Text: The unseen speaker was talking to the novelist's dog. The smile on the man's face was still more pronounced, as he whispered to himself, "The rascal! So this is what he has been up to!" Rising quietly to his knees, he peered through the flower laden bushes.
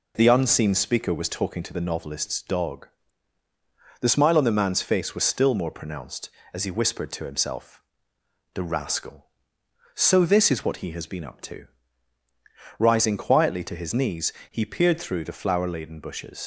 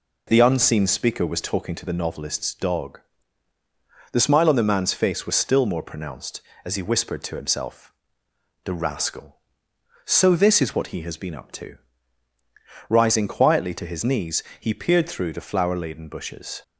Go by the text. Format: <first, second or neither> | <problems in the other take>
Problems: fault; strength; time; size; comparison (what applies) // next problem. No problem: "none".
second | leaves "bushes" unfinished; at 16.4 s; 75 ms